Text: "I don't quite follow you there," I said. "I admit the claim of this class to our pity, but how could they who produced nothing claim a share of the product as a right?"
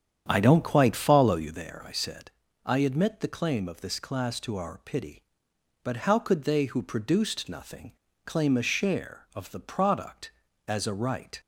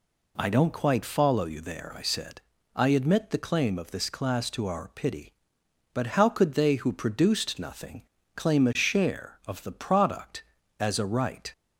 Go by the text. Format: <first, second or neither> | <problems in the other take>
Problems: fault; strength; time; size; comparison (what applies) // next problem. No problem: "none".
second | starts louder than the rest; strong; until 1.6 s; 9 dB // pauses between "nothing" and "claim"; slight; at 7.9 s; 0.32 s long; slight in the second